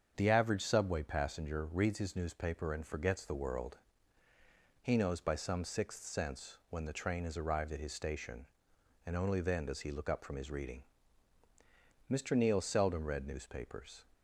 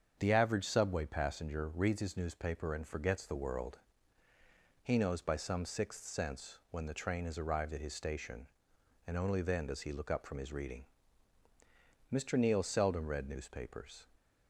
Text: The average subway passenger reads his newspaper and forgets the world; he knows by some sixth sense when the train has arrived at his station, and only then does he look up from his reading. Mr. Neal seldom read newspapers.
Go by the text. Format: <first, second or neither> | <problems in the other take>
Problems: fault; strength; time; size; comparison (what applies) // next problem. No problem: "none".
neither | starts louder than the rest; strong; the same in both